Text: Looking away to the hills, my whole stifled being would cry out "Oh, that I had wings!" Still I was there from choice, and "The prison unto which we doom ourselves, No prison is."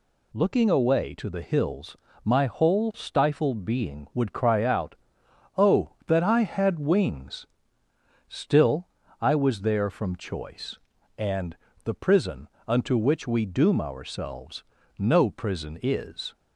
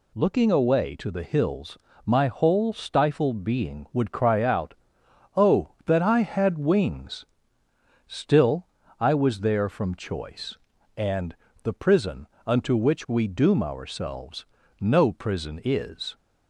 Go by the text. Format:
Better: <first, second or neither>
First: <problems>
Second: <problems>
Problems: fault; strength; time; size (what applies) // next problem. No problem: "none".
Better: neither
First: pauses between "out" and "Oh"; noticeable; at 4.9 s; 0.62 s long // pauses between "Still" and "I"; slight; at 8.8 s; 0.34 s long // pauses between "and" and "The"; slight; at 11.5 s; 0.26 s long // pauses between "prison" and "unto"; slight; at 12.4 s; 0.18 s long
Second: pauses between "out" and "Oh"; noticeable; at 4.7 s; 0.62 s long // pauses between "Still" and "I"; slight; at 8.6 s; 0.34 s long // pauses between "and" and "The"; slight; at 11.3 s; 0.26 s long // pauses between "prison" and "unto"; slight; at 12.2 s; 0.18 s long